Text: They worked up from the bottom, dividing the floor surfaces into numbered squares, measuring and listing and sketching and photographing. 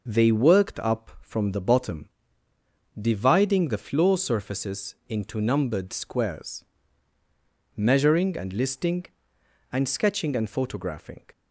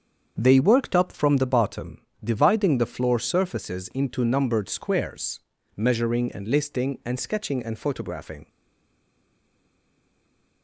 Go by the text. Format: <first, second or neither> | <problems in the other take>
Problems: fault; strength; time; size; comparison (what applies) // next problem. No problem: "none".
first | starts louder than the rest; until 1.4 s; 7 dB // stays silent after the last word; from 8.4 s on; 2.2 s long